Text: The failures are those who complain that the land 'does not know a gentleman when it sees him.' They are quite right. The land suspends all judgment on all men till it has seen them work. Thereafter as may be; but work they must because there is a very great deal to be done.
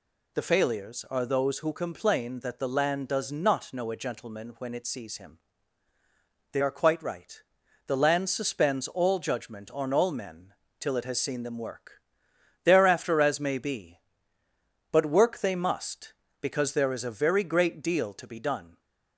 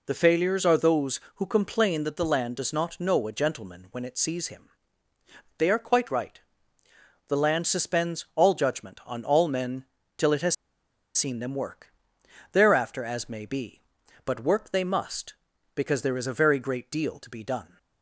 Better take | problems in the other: first | pauses between "men" and "till"; slight; at 9.8 s; 0.32 s long; slight in the first // pauses between "has" and "seen"; noticeable; at 10.5 s; 0.62 s long

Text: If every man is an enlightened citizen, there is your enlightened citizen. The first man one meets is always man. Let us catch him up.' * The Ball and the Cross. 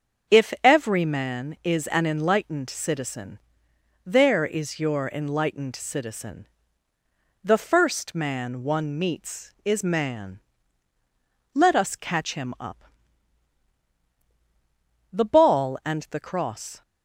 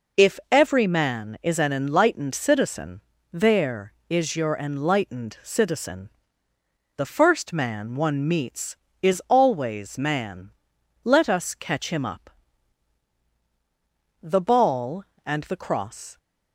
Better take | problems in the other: second | starts louder than the rest; until 1.4 s; 6.5 dB // skips "always"; at 9.8 s

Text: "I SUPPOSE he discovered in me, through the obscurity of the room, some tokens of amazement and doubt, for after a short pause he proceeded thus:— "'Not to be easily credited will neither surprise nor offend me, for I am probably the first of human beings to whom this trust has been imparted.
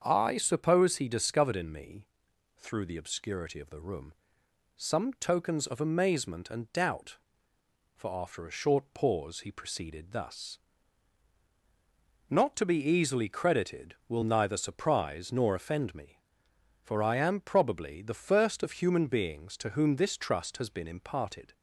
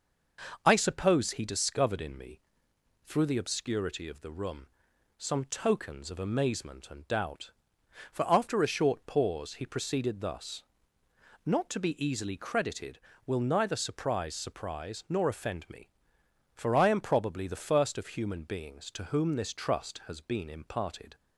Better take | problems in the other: first | starts louder than the rest; noticeable; until 1.6 s; 6 dB; also in the first // says "surprise" twice; at 14.3 s

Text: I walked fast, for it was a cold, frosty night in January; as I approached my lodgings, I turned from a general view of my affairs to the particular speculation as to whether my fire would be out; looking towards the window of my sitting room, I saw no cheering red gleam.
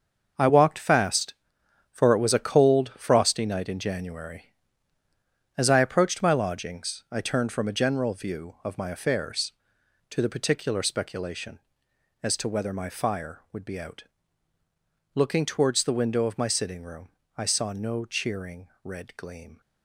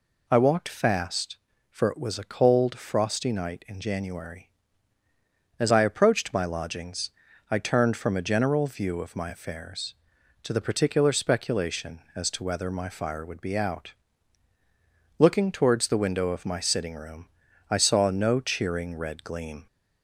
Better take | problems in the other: second | gets quieter; strong; throughout; 10 dB // pauses between "cheering" and "red"; slight; at 18.6 s; 0.16 s long

